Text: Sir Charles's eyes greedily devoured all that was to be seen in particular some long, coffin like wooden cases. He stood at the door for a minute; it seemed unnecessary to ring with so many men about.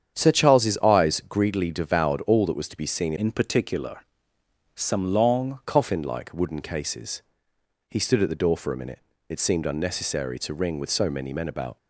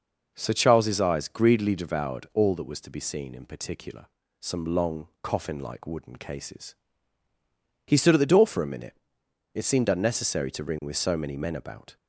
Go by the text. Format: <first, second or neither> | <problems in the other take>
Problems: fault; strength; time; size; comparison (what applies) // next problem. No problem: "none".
second | starts louder than the rest; strong; until 1.1 s; 8.5 dB // changes voice from "in" to "long"; from 3.1 to 5.5 s; 2.4 s long // pauses between "particular" and "some"; noticeable; at 3.9 s; 0.74 s long; slight in the second